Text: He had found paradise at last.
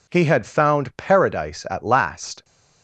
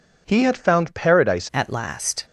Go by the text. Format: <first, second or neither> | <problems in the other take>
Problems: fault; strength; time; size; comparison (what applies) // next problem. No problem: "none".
first | changes voice at "at"; from 1.5 s on; 0.7 s long